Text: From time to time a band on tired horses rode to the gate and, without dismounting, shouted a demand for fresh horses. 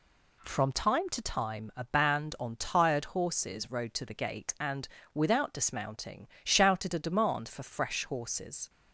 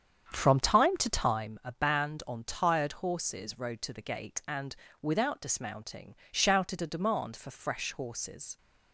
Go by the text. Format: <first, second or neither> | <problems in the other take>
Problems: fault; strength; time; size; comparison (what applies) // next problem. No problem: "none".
first | starts louder than the rest; strong; until 1.5 s; 8 dB